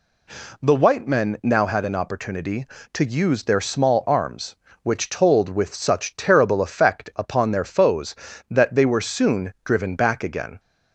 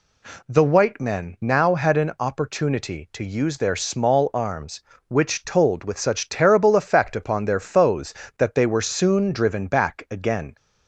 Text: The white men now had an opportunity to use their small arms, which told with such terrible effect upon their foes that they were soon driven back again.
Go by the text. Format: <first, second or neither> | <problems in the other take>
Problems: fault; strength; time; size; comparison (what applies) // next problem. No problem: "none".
neither | none